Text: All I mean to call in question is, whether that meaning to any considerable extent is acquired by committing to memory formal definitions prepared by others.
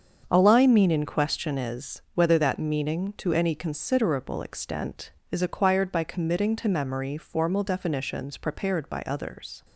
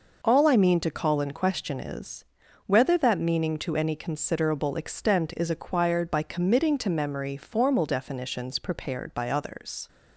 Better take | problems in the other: second | starts louder than the rest; until 1.3 s; 7 dB // skips "to call"; at 0.9 s

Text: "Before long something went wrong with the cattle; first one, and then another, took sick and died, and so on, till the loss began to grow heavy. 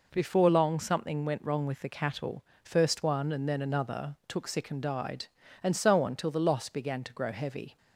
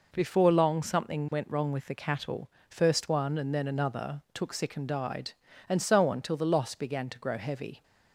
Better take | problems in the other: neither | none

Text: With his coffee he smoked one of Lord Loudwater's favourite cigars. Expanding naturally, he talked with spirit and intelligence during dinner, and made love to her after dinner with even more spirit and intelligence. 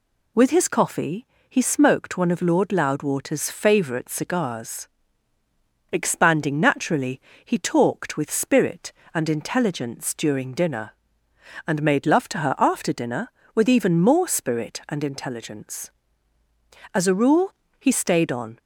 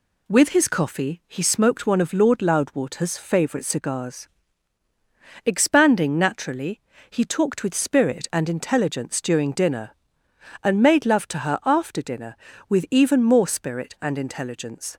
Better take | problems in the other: second | pauses between "coffee" and "he"; slight; at 1.2 s; 0.22 s long // goes on to say "As a rule he stayed on"; from 16.9 s on; 1.6 s long

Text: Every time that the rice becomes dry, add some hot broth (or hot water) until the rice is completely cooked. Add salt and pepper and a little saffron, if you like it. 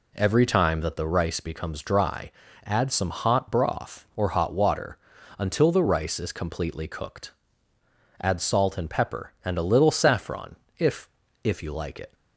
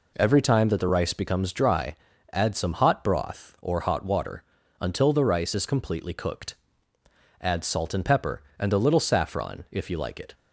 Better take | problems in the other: second | says "if" twice; at 11.4 s

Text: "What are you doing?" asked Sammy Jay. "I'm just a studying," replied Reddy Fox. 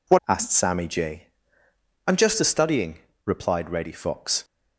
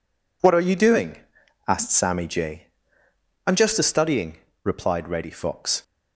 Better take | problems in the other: second | skips "are you doing"; at 0.2 s

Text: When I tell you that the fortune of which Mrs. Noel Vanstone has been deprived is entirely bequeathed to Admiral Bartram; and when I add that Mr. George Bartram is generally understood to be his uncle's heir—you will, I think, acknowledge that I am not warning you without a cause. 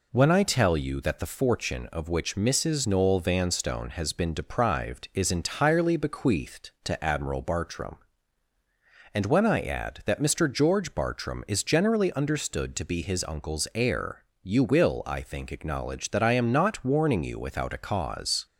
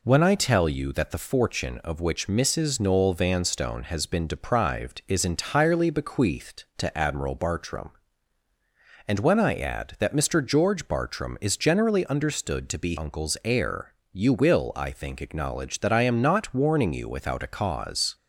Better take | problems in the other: first | skips "his"; at 12.9 s

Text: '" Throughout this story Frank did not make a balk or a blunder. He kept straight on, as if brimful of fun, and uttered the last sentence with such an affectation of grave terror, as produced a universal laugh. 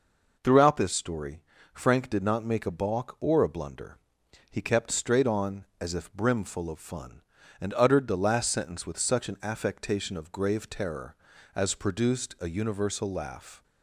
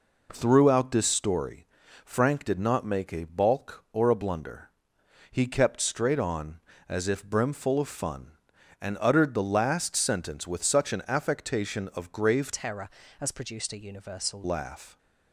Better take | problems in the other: first | pauses between "story" and "Frank"; at 1.6 s; 0.38 s long; slight in the first // changes voice from "terror" to "universal"; from 12.5 to 14.4 s; 1.9 s long

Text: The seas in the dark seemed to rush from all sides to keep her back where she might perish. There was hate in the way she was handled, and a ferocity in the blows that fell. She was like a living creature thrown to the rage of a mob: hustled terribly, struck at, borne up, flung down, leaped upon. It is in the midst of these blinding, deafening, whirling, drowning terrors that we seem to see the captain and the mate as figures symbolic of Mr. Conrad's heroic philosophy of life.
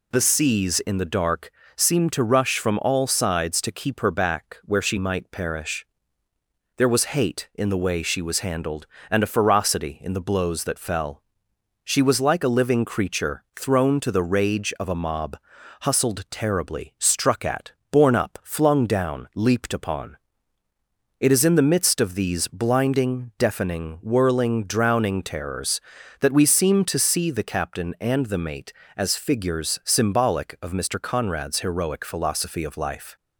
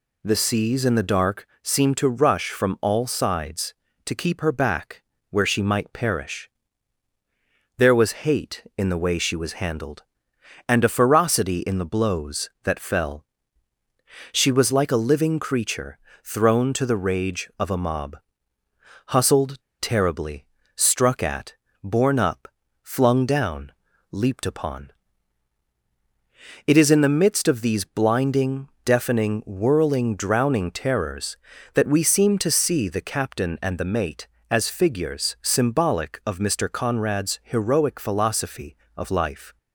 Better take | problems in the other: first | pauses between "dark" and "seemed"; slight; at 1.4 s; 0.16 s long; slight in the first // pauses between "back" and "where"; slight; at 5.0 s; 0.30 s long // pauses between "creature" and "thrown"; slight; at 15.9 s; 0.26 s long // pauses between "hustled" and "terribly"; slight; at 19.5 s; 0.24 s long

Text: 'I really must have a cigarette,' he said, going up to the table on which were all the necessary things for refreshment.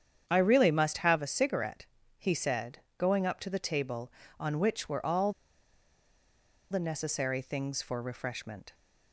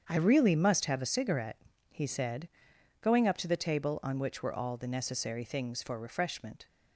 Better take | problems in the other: second | starts louder than the rest; strong; until 1.2 s; 8.5 dB; strong in the second // pauses between "all" and "the"; strong; at 5.3 s; 1.4 s long

